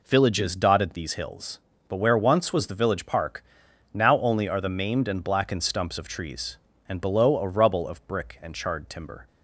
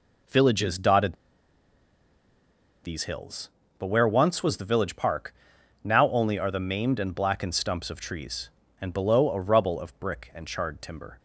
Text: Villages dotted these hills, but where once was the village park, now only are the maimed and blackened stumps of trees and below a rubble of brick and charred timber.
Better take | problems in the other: first | pauses between "dotted" and "these"; strong; at 1.1 s; 1.7 s long

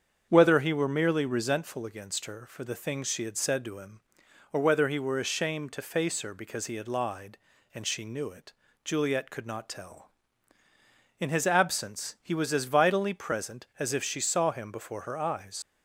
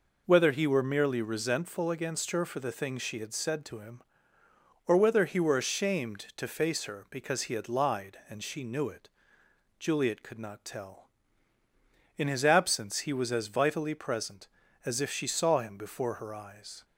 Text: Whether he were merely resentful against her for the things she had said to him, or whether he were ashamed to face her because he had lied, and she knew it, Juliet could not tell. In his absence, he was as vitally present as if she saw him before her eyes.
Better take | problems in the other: second | starts louder than the rest; strong; until 1.3 s; 7.5 dB // leaves "eyes" unfinished; at 15.6 s; 75 ms

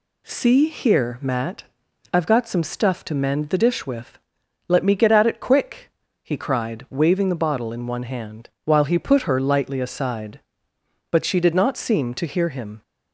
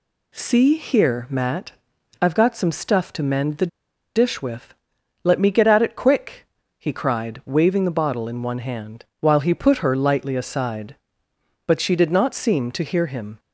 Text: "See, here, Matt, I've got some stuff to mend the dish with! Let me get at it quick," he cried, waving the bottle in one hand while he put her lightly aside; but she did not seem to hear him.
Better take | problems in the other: first | pauses between "the" and "dish"; noticeable; at 3.6 s; 0.48 s long // pauses between "hand" and "while"; slight; at 9.0 s; 0.16 s long; slight in the first

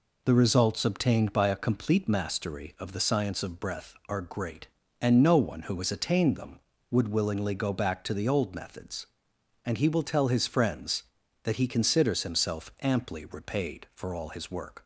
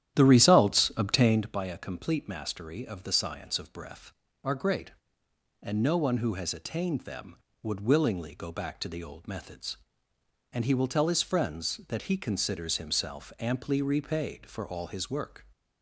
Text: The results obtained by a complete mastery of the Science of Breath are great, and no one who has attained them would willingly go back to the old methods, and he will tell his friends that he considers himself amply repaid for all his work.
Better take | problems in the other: first | starts louder than the rest; strong; until 1.5 s; 11.5 dB

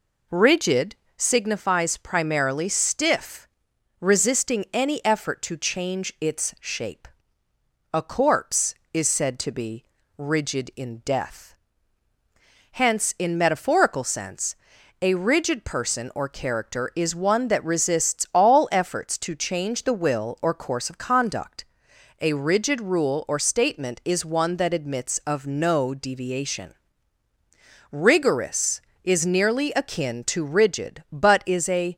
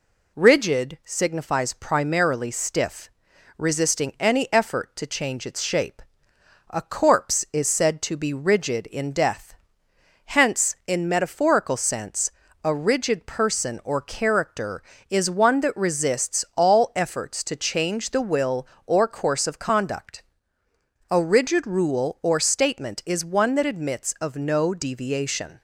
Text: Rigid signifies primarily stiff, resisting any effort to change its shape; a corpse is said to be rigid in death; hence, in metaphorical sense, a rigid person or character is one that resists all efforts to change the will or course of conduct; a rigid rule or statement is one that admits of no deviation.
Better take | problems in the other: second | pauses between "Rigid" and "signifies"; slight; at 0.9 s; 0.20 s long // pauses between "be" and "rigid"; slight; at 9.8 s; 0.34 s long // goes on to say "Rigorous is nearly akin to rigid but is a"; strong; from 27.9 s on; 4.0 s long

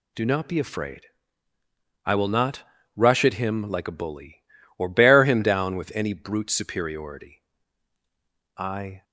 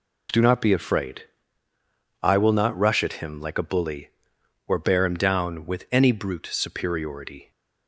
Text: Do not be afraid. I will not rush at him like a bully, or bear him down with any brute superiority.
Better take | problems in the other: second | pauses between "not" and "rush"; slight; at 2.6 s; 0.34 s long // goes on to say "I"; slight; from 8.5 s on; 0.46 s long

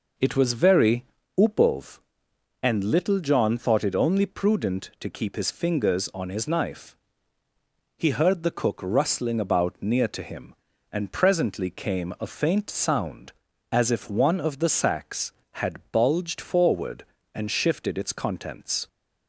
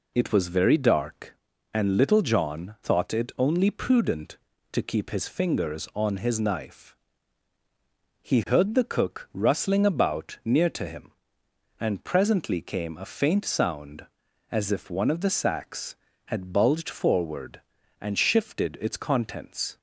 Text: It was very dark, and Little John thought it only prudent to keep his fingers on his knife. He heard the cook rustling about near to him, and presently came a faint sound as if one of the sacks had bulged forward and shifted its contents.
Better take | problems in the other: second | says "upov" for "dark"; at 1.3 s

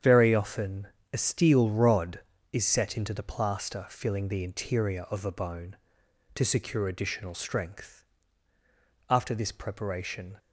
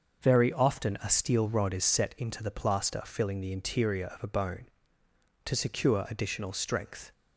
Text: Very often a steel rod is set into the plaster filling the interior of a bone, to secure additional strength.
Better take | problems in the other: second | starts louder than the rest; strong; until 1.3 s; 8.5 dB; also in the second // pauses between "often" and "a"; slight; at 0.8 s; 0.26 s long // goes on to say "After this preparation"; noticeable; from 9.0 s on; 1.2 s long

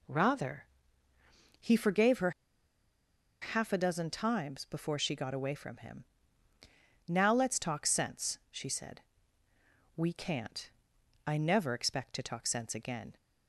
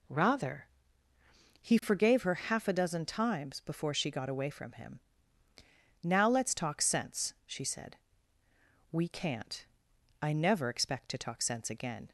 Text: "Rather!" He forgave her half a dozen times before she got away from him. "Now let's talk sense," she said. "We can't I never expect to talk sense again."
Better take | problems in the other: second | pauses between "her" and "half"; at 2.3 s; 1.1 s long // pauses between "can't" and "I"; noticeable; at 10.6 s; 0.56 s long; noticeable in the second

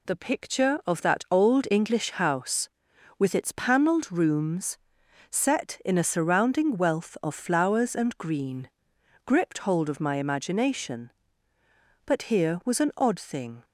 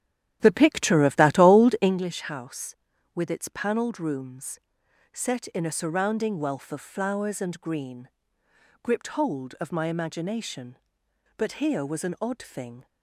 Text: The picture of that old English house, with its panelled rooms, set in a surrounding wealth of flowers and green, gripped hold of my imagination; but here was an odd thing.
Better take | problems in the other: first | starts louder than the rest; strong; until 2.0 s; 11 dB

